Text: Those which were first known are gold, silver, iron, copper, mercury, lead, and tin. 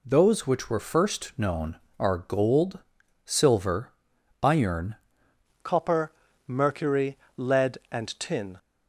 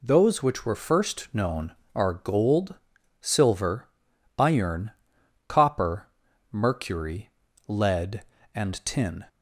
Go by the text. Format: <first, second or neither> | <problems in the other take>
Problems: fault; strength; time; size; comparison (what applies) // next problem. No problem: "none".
second | changes voice at "copper"; from 5.6 s on; 2.9 s long